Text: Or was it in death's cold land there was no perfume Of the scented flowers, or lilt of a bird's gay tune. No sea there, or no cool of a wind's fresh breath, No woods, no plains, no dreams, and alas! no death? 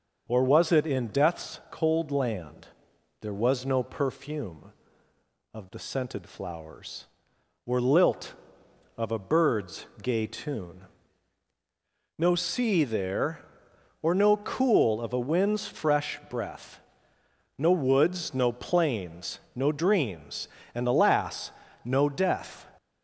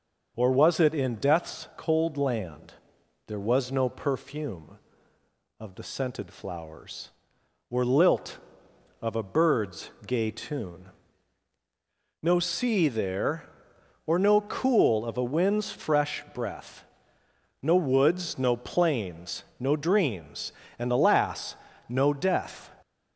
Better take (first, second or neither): neither